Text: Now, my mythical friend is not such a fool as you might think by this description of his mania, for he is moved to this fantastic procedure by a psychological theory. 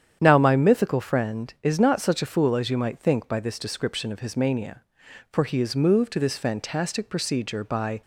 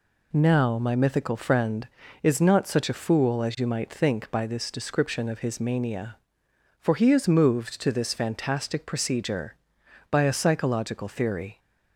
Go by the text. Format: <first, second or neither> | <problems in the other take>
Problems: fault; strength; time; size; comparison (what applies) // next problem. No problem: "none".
second | starts louder than the rest; strong; until 1.2 s; 9 dB // stops before "a psychological theory"; at 8.0 s